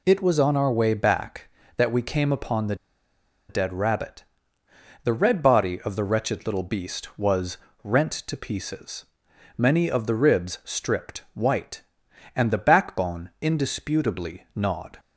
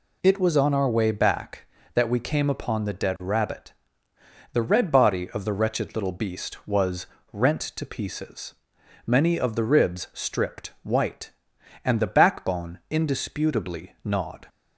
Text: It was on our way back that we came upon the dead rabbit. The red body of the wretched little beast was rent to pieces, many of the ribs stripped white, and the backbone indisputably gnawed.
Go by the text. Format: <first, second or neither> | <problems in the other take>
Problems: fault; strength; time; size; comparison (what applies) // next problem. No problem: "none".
second | pauses between "the" and "dead"; noticeable; at 2.7 s; 0.74 s long // pauses between "was" and "rent"; slight; at 7.5 s; 0.28 s long; slight in the second